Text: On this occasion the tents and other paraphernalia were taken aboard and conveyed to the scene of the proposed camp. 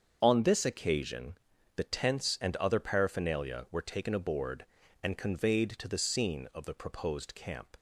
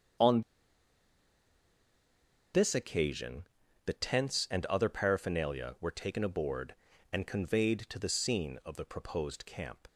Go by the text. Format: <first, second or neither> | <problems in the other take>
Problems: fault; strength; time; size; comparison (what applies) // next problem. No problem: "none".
first | starts louder than the rest; until 3.3 s; 7 dB; also in the first // pauses between "On" and "this"; strong; at 0.4 s; 2.1 s long // pauses between "occasion" and "the"; at 3.4 s; 0.40 s long; also in the first